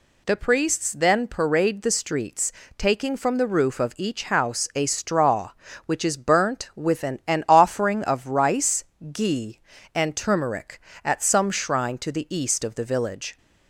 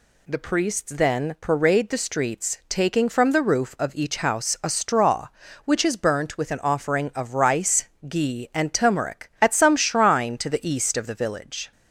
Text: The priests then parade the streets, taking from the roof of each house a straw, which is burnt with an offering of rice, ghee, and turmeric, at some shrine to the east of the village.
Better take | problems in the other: second | says "an" twice; at 7.2 s

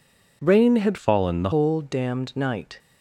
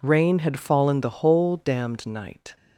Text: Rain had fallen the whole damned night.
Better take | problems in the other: second | changes voice from "fallen" to "the"; from 0.9 to 1.4 s; 0.5 s long

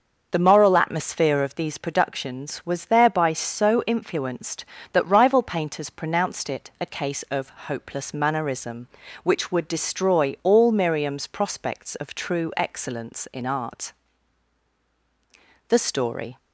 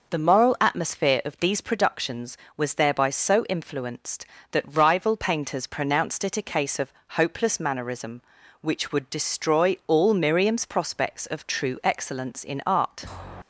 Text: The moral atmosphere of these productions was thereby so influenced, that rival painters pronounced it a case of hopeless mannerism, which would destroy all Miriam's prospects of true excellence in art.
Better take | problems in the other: second | starts louder than the rest; until 1.3 s; 6 dB // pauses between "of" and "hopeless"; slight; at 7.5 s; 0.18 s long; slight in the second // goes on to say "The story"; noticeable; from 15.6 s on; 0.68 s long

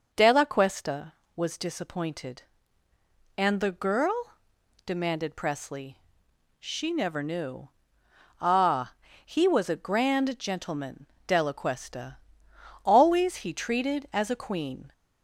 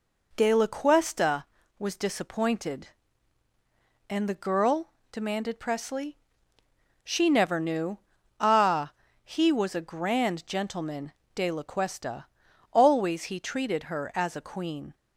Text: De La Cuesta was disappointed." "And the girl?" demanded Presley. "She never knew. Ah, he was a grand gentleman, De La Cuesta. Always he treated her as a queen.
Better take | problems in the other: second | skips "her"; at 14.0 s

